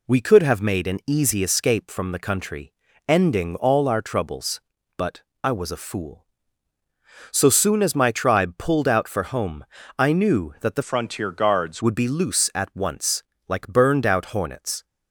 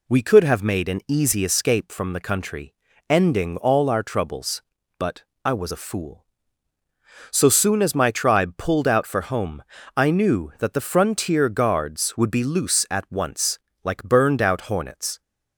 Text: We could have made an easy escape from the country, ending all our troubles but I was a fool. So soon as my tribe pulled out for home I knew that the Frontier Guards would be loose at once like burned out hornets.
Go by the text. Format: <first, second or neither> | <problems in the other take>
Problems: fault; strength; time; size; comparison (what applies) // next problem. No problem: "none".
second | pauses between "but" and "I"; slight; at 5.2 s; 0.20 s long; slight in the second // pauses between "home" and "I"; slight; at 9.6 s; 0.32 s long; slight in the second // changes voice from "Frontier" to "Guards"; from 10.8 to 11.8 s; 1.0 s long // pauses between "once" and "like"; slight; at 13.2 s; 0.24 s long; slight in the second